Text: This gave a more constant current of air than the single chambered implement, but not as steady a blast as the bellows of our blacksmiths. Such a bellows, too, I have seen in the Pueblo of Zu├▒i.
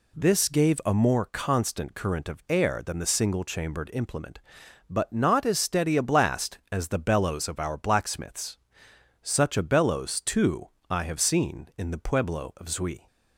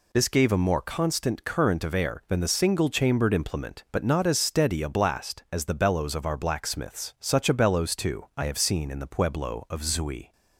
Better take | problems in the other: neither | none

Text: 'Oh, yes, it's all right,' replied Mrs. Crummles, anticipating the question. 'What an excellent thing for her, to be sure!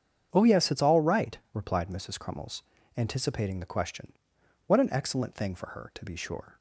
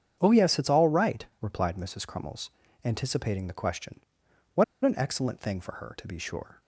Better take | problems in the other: first | starts louder than the rest; strong; until 1.2 s; 8 dB; strong in the first // pauses between "What" and "an"; slight; at 4.6 s; 0.20 s long

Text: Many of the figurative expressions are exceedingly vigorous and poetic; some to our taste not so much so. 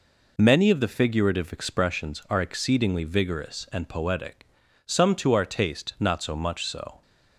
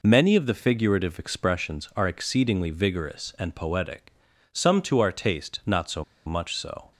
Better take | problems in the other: first | pauses between "so" and "much"; slight; at 6.0 s; 0.22 s long

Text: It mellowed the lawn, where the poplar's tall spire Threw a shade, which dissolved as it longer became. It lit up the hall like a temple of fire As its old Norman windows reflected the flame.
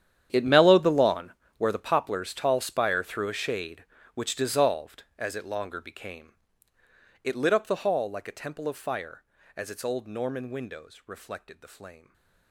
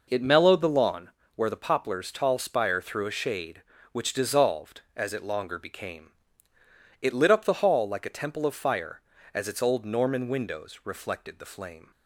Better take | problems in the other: second | gets quieter; strong; throughout; 17.5 dB // stays silent after the last word; slight; from 11.9 s on; 0.6 s long

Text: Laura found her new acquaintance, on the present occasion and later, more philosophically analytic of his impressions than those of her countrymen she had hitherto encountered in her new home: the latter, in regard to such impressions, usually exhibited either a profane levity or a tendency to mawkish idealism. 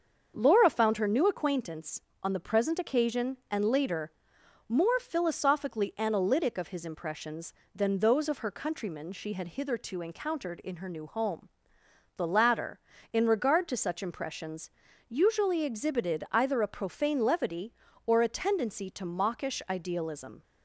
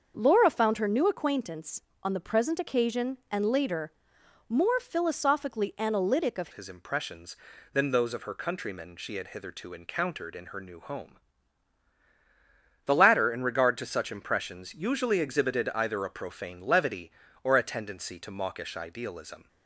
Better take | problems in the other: first | starts louder than the rest; until 1.1 s; 6.5 dB; also in the first // changes voice at "his"; from 6.5 s on; 12.9 s long

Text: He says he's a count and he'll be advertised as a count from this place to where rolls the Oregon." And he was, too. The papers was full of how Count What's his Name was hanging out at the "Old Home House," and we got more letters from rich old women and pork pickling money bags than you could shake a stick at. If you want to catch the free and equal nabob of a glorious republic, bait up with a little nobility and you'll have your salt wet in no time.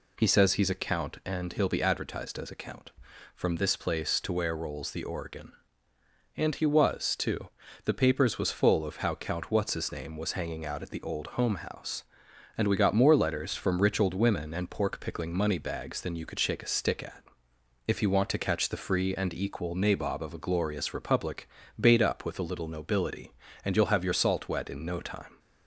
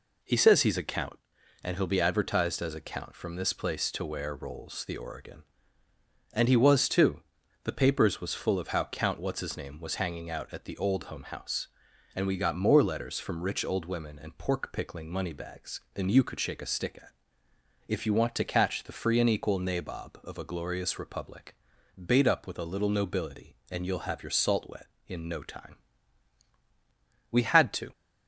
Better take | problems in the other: first | goes on to say "We had to"; noticeable; from 27.2 s on; 0.62 s long

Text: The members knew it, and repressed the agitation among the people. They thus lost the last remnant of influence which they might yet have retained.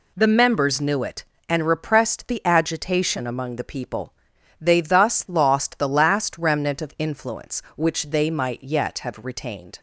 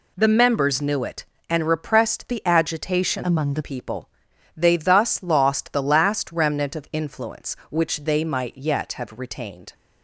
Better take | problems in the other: first | changes voice from "among" to "the"; from 3.2 to 3.6 s; 0.4 s long

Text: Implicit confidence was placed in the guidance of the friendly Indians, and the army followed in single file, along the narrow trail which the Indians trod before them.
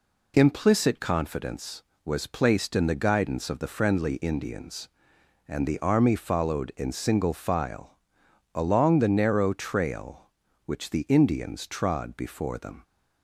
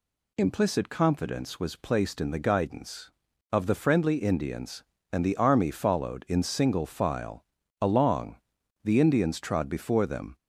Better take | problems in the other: first | pauses between "along" and "the"; noticeable; at 8.3 s; 0.46 s long // skips "narrow trail which the"; at 8.9 s

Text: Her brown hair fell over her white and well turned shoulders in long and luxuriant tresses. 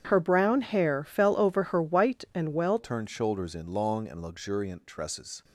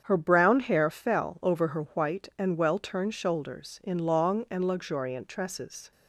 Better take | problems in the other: second | starts louder than the rest; strong; until 1.1 s; 8.5 dB; strong in the second // changes voice at "turned"; from 2.7 s on; 2.7 s long

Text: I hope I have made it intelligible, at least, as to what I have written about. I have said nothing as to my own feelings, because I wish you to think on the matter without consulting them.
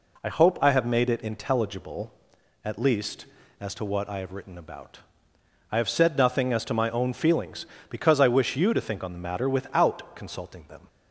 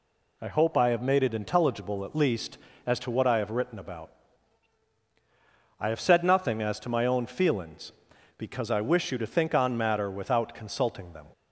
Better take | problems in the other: first | skips "the"; at 9.7 s

